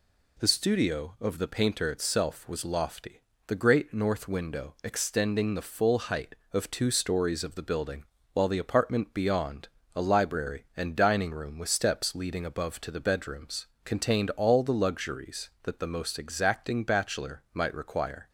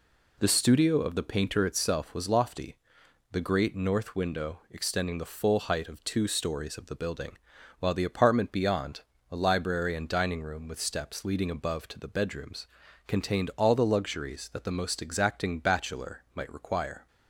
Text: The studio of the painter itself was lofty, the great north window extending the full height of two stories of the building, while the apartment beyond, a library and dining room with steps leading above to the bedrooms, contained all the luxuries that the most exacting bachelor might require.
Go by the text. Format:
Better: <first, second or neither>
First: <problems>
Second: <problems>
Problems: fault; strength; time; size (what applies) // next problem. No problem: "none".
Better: neither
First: none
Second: none